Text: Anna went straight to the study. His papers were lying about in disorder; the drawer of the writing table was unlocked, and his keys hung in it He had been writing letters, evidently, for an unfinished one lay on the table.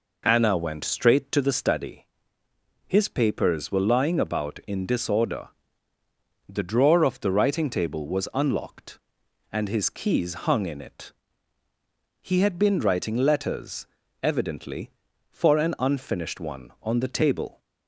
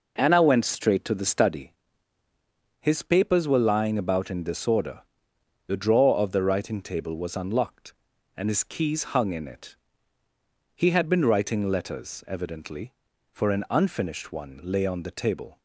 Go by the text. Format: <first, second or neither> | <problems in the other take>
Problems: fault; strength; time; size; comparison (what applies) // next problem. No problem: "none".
second | pauses between "it" and "He"; at 11.1 s; 1.1 s long; noticeable in the second // skips "lay"; at 16.7 s